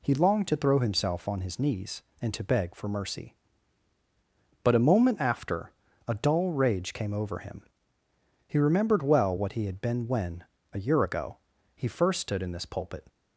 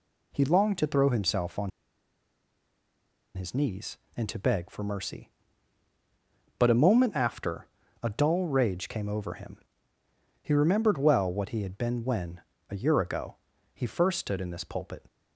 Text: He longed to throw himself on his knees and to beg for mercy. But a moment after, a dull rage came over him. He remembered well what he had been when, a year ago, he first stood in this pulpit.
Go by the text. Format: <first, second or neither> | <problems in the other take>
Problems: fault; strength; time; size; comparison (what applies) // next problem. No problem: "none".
first | pauses between "on" and "his"; strong; at 1.7 s; 1.6 s long